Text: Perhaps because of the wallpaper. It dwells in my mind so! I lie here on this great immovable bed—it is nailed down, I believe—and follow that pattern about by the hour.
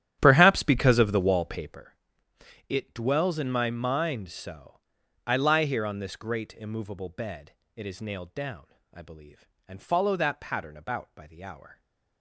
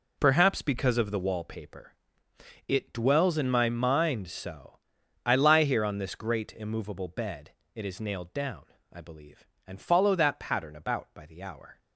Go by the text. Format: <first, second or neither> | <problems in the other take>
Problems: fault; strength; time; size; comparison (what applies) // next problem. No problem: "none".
second | starts louder than the rest; strong; until 1.8 s; 11 dB